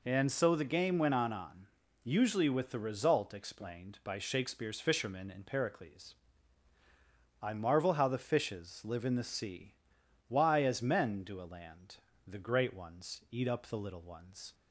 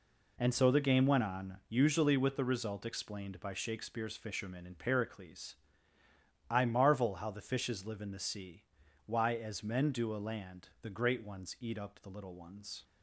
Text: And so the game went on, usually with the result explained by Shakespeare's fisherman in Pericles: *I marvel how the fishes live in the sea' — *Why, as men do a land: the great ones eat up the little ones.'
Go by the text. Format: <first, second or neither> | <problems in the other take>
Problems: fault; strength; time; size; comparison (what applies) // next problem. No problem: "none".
second | says "on" twice; at 1.3 s